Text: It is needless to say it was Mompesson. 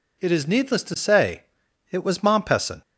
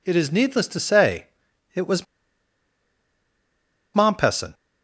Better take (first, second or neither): first